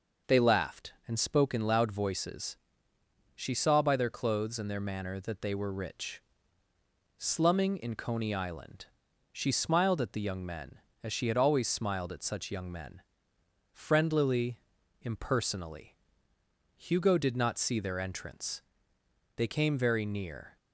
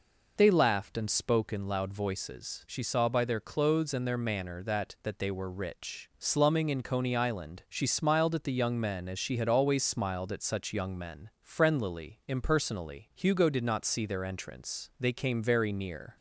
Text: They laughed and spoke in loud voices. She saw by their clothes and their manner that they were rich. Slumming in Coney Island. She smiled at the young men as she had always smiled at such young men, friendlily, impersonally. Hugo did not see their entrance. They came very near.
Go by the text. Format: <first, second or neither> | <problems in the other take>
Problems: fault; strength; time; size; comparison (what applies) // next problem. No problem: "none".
first | says "that" twice; at 5.0 s